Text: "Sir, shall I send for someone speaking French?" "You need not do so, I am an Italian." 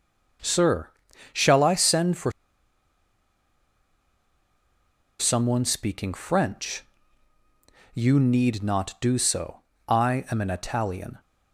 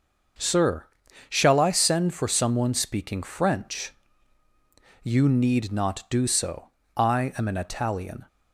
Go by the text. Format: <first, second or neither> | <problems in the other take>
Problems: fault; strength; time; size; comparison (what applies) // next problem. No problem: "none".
second | starts louder than the rest; until 1.8 s; 6.5 dB; also in the second // pauses between "for" and "someone"; strong; at 2.3 s; 2.8 s long